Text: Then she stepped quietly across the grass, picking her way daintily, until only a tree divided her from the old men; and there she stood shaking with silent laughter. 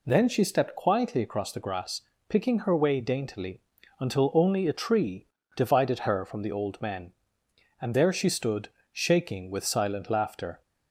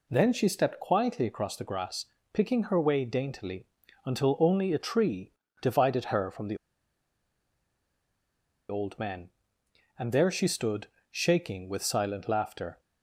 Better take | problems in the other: first | pauses between "tree" and "divided"; slight; at 5.3 s; 0.30 s long; slight in the first // pauses between "the" and "old"; strong; at 6.5 s; 2.1 s long // pauses between "stood" and "shaking"; slight; at 10.8 s; 0.24 s long; slight in the first

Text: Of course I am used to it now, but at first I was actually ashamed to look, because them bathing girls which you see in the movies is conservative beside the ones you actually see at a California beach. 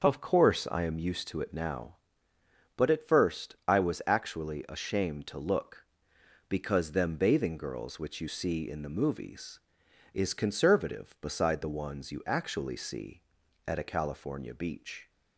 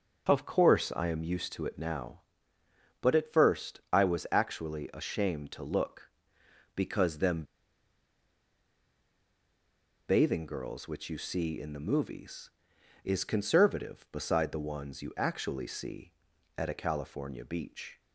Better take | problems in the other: first | starts louder than the rest; noticeable; until 1.3 s; 6 dB; noticeable in the first // pauses between "them" and "bathing"; strong; at 7.4 s; 2.6 s long

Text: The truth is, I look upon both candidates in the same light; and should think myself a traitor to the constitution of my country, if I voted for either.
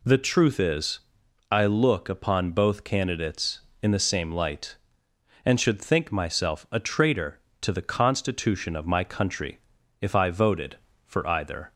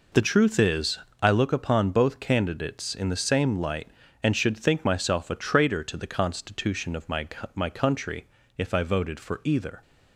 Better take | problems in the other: first | says "my" twice; at 7.5 s

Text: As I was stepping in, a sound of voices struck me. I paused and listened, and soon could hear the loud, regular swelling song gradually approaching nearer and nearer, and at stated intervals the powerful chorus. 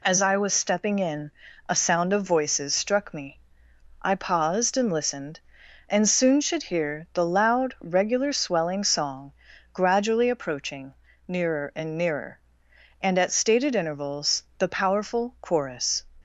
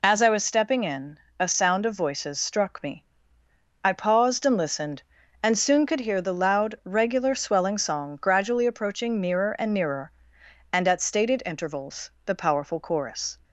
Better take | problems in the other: second | says "should" for "could"; at 6.4 s // pauses between "song" and "gradually"; at 9.3 s; 0.42 s long // pauses between "approaching" and "nearer"; slight; at 10.9 s; 0.32 s long // pauses between "intervals" and "the"; slight; at 14.4 s; 0.16 s long

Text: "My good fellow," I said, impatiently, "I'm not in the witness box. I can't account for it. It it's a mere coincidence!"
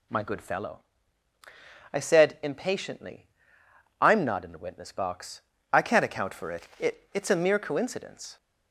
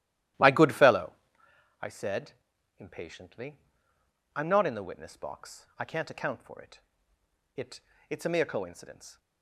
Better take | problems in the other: first | starts louder than the rest; strong; until 1.6 s; 13.5 dB // pauses between "It" and "it's"; slight; at 7.7 s; 0.32 s long

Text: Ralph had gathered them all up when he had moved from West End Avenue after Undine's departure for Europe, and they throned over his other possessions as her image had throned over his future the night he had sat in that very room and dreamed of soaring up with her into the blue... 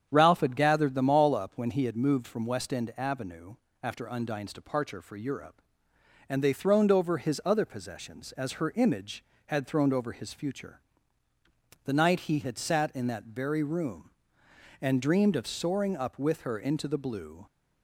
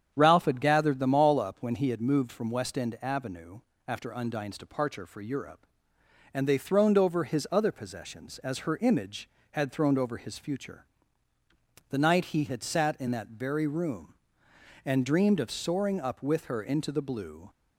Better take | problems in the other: neither | starts louder than the rest; strong; the same in both // pauses between "Avenue" and "after"; slight; the same in both // pauses between "future" and "the"; the same in both

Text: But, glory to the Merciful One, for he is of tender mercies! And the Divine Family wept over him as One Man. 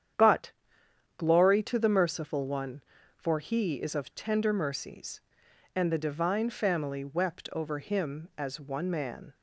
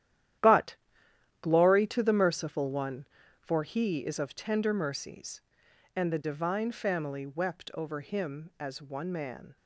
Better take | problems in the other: first | gets quieter; strong; throughout; 11 dB // starts louder than the rest; strong; until 2.0 s; 11.5 dB; strong in the first

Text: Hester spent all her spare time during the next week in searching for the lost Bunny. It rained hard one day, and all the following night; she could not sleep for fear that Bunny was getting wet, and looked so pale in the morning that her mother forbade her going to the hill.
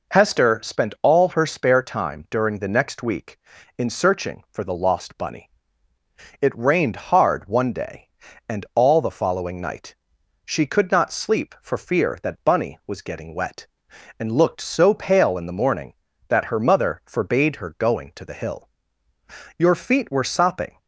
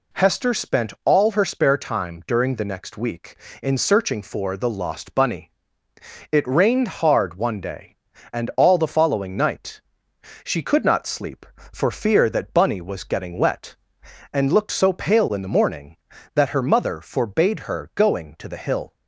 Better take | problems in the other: second | goes on to say "Your feet were sopping"; noticeable; from 19.5 s on; 1.2 s long

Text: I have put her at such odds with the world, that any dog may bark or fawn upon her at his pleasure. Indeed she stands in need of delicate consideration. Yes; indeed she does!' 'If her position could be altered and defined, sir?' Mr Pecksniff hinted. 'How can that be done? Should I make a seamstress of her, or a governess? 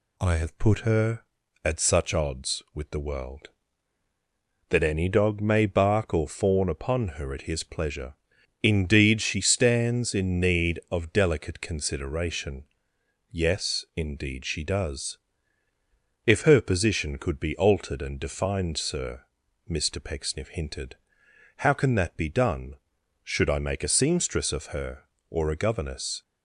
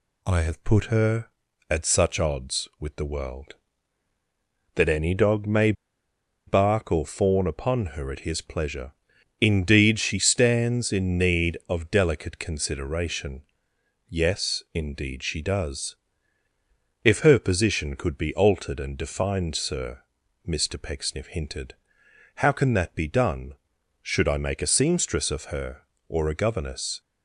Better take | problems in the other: first | pauses between "may" and "bark"; noticeable; at 5.7 s; 0.74 s long

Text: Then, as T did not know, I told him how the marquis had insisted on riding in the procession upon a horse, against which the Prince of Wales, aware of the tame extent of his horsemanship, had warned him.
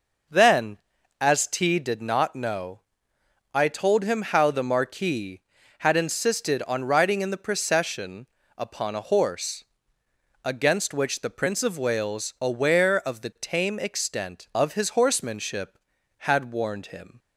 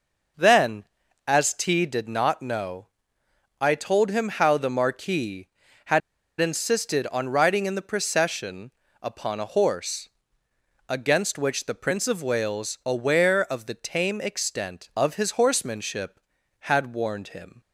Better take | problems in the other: first | pauses between "had" and "insisted"; at 6.0 s; 0.39 s long // pauses between "procession" and "upon"; slight; at 8.7 s; 0.32 s long; slight in the first

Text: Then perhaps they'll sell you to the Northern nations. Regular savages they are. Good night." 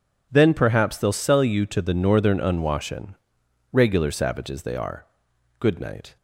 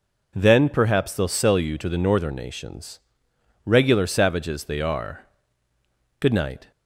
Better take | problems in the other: second | says "unwashen" for "nations"; at 2.3 s

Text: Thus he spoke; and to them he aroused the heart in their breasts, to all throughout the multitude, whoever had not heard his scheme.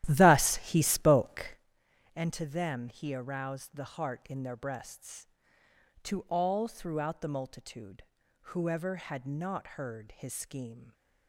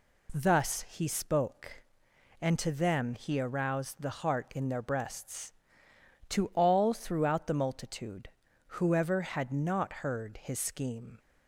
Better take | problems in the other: second | starts louder than the rest; strong; until 1.7 s; 12.5 dB

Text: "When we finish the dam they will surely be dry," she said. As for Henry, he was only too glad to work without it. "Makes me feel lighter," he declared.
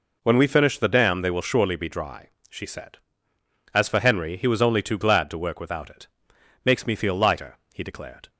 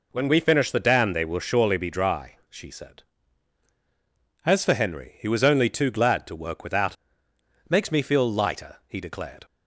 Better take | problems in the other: first | skips "it"; at 7.3 s

